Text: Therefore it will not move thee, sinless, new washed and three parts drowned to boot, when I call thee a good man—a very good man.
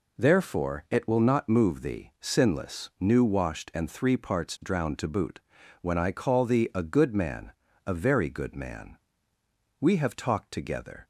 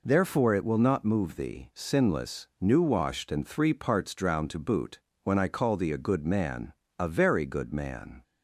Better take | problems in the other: second | goes on to say "We have talked together"; noticeable; from 9.8 s on; 1.2 s long

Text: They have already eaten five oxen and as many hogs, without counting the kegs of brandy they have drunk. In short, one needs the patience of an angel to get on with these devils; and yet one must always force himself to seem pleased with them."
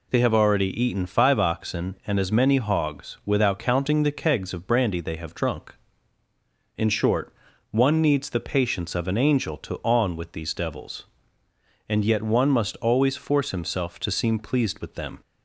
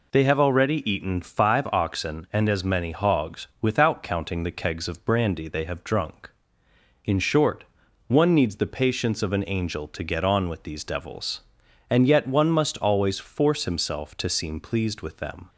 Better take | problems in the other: second | skips "get"; at 9.8 s

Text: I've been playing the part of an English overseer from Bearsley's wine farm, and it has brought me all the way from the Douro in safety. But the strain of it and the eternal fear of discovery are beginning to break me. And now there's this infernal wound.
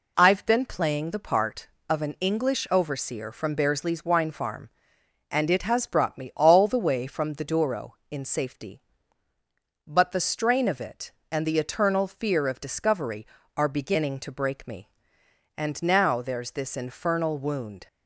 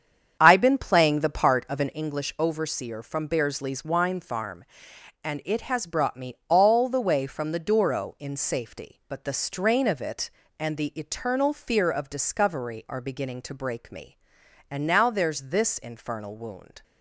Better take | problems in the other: first | starts louder than the rest; strong; until 2.0 s; 8 dB

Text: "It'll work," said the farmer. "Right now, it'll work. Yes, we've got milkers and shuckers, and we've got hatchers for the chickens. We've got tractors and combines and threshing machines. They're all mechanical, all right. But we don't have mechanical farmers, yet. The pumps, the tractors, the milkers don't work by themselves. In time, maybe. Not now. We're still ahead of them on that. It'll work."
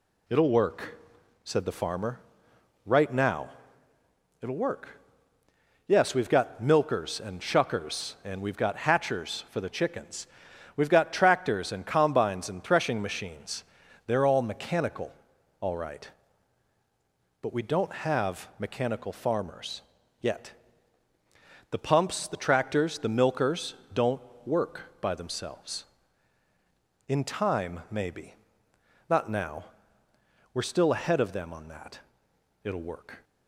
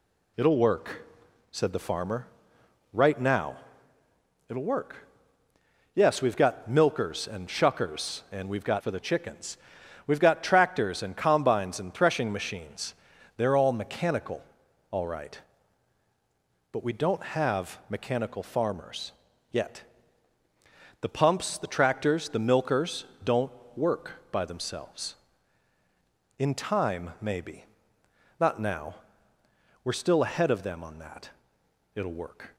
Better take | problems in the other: first | skips "hatchers"; at 8.8 s // pauses between "milkers" and "don't"; slight; at 23.0 s; 0.18 s long; slight in the first // pauses between "don't" and "work"; slight; at 23.5 s; 0.26 s long; slight in the first

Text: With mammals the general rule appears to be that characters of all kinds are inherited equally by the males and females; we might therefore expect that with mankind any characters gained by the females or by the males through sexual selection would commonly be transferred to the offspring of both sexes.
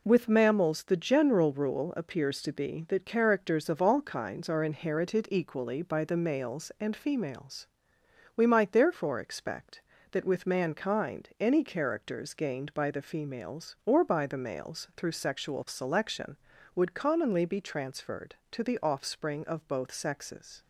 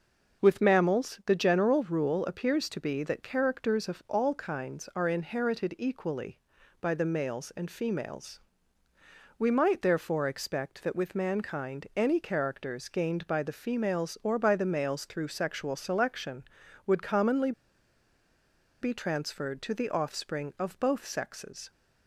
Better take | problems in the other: first | pauses between "commonly" and "be"; strong; at 17.5 s; 1.3 s long

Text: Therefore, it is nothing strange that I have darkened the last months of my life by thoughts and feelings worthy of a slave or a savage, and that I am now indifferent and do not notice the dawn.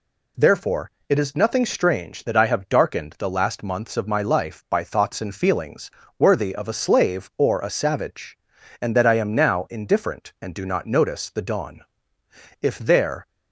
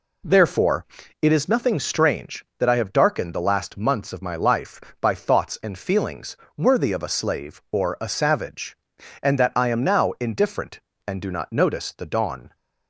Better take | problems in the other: second | pauses between "feelings" and "worthy"; slight; at 5.9 s; 0.28 s long; slight in the second // goes on to say "If there"; noticeable; from 12.6 s on; 0.66 s long

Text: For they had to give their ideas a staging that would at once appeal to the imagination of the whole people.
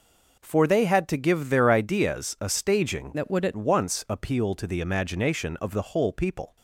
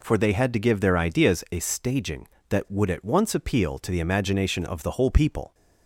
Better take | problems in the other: second | changes voice from "that" to "at"; from 3.1 to 3.5 s; 0.4 s long

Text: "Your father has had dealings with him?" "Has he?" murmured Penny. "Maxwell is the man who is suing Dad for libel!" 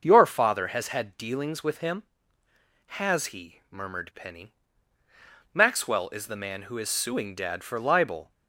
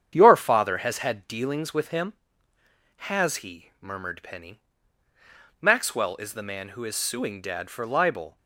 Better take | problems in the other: first | gets quieter; noticeable; throughout; 5 dB // starts louder than the rest; strong; until 1.1 s; 8.5 dB; noticeable in the first

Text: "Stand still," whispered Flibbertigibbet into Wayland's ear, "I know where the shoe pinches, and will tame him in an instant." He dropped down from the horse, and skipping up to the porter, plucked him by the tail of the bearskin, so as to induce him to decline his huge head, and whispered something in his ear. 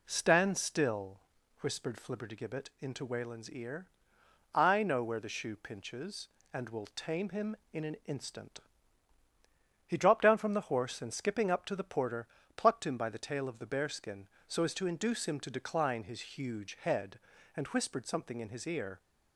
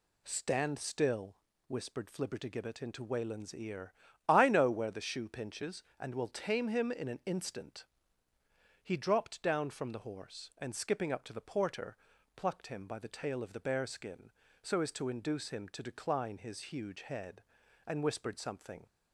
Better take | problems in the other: first | stops before "in his ear"; at 18.8 s

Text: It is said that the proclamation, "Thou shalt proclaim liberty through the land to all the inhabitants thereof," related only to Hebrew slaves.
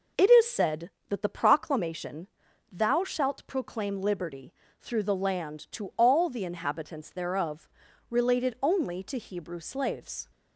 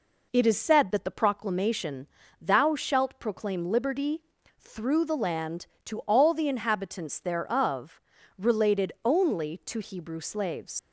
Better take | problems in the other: first | pauses between "liberty" and "through"; at 4.2 s; 0.38 s long; slight in the first // leaves "slaves" unfinished; at 10.7 s; 75 ms

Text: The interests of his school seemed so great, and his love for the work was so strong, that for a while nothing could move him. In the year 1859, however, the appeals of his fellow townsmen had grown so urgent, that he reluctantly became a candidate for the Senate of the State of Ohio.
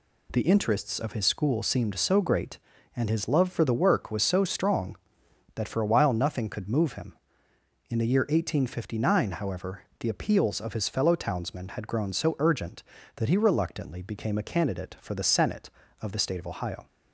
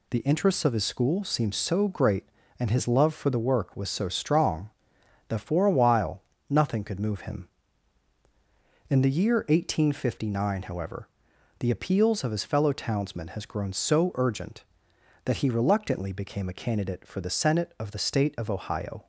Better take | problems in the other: first | pauses between "while" and "nothing"; slight; at 6.2 s; 0.26 s long // says "has" for "had"; at 13.2 s

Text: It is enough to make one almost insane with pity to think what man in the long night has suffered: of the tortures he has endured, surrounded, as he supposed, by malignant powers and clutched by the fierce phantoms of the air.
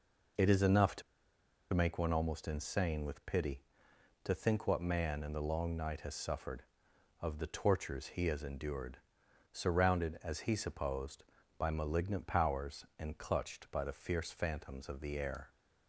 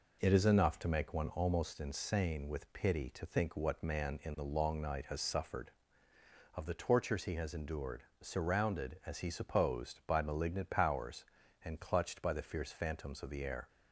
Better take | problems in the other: second | pauses between "to" and "make"; noticeable; at 1.0 s; 0.71 s long

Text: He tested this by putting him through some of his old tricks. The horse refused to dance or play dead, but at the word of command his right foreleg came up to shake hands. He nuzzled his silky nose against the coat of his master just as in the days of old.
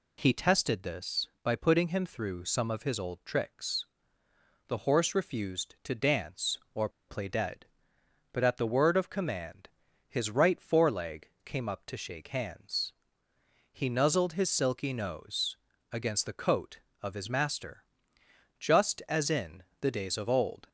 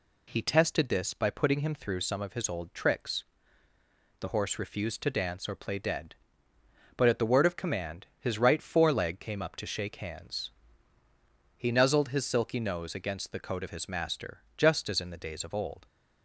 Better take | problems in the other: second | pauses between "or" and "play"; slight; at 6.8 s; 0.19 s long // pauses between "command" and "his"; at 9.6 s; 0.40 s long; slight in the second // pauses between "foreleg" and "came"; slight; at 11.2 s; 0.16 s long // pauses between "nose" and "against"; slight; at 15.5 s; 0.34 s long // pauses between "master" and "just"; noticeable; at 17.8 s; 0.76 s long; slight in the second // pauses between "in" and "the"; slight; at 19.6 s; 0.18 s long

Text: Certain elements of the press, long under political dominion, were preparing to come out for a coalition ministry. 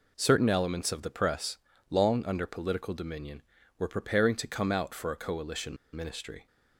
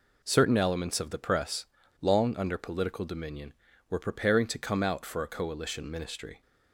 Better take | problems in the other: second | pauses between "coalition" and "ministry"; slight; at 5.7 s; 0.18 s long

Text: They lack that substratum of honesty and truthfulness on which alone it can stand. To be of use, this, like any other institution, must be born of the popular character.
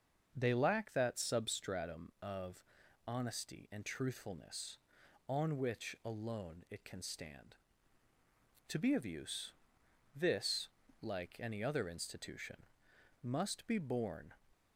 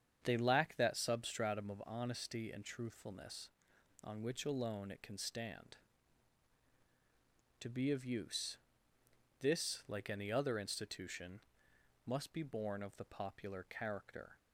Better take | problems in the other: second | starts louder than the rest; until 1.3 s; 6.5 dB; strong in the second // pauses between "of" and "honesty"; at 2.6 s; 0.42 s long // stops before "of the popular character"; at 14.5 s

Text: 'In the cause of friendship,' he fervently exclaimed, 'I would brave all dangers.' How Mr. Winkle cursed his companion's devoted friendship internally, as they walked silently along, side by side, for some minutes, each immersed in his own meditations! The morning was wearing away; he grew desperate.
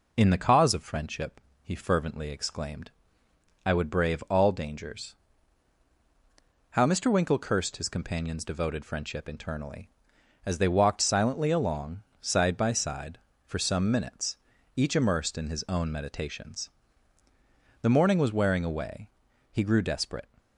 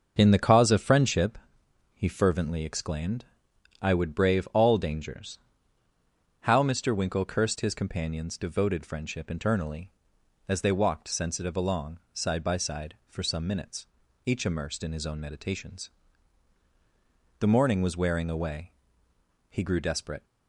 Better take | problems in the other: first | starts louder than the rest; until 1.1 s; 6.5 dB // says "sensitive" for "silently"; at 11.0 s

